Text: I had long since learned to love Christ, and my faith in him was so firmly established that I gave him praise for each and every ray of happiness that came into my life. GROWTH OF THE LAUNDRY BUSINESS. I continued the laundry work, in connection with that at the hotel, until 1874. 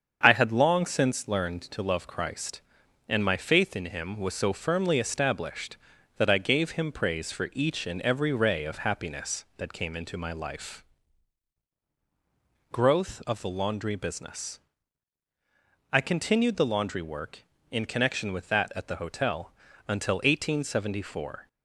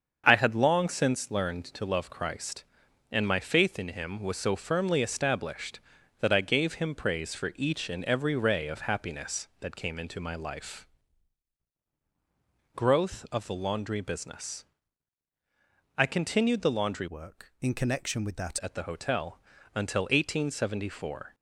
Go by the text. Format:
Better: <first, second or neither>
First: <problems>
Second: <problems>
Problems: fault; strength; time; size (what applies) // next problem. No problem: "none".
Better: first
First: starts louder than the rest; until 1.2 s; 7 dB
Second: starts louder than the rest; until 1.2 s; 7 dB // changes voice from "work" to "that"; from 17.0 to 18.5 s; 1.5 s long